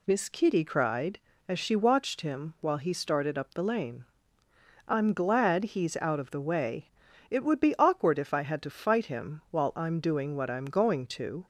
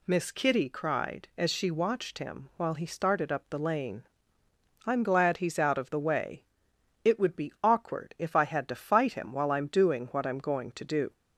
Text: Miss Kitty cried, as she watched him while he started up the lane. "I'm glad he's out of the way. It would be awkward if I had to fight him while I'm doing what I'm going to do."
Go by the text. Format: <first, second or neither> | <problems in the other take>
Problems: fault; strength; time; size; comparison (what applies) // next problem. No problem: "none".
second | stops before "do"; at 11.4 s